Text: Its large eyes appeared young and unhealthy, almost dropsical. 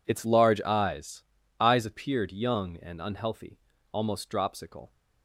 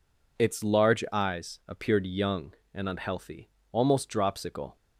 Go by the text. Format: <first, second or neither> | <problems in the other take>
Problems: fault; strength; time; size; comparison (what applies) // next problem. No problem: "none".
second | says "eyes" twice; at 1.6 s